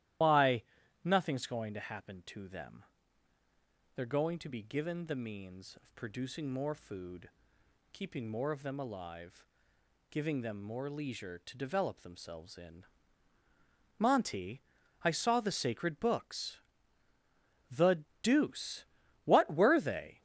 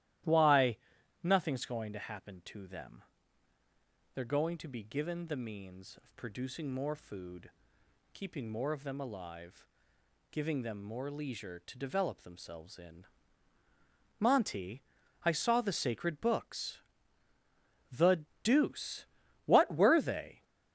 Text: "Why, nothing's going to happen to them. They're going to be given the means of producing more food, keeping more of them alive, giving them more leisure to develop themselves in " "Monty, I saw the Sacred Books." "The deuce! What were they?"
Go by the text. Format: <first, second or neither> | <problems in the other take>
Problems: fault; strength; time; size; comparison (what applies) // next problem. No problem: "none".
second | loses the start of "Why"; at 0.2 s; 105 ms // starts louder than the rest; strong; until 1.6 s; 13.5 dB; strong in the second // pauses between "The" and "deuce"; slight; at 18.0 s; 0.18 s long; slight in the second